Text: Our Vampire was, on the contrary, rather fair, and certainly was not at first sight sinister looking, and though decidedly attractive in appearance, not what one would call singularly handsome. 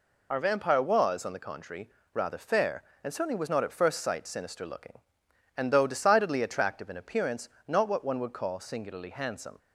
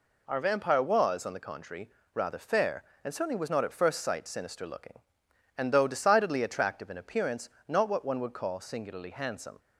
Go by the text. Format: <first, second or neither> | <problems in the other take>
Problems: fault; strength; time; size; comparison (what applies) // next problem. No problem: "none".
second | loses the start of "Our"; at 0.3 s; 30 ms